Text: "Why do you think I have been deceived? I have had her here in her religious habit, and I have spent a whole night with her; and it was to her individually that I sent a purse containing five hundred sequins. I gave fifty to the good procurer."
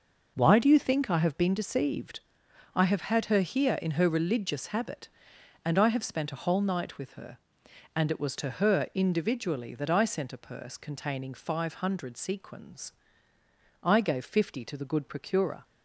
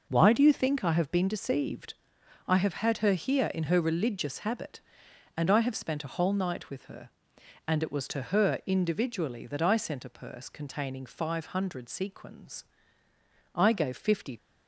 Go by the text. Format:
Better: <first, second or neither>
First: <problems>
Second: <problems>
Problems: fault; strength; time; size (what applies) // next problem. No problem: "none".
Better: first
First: none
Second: stops before "to the good procurer"; at 14.3 s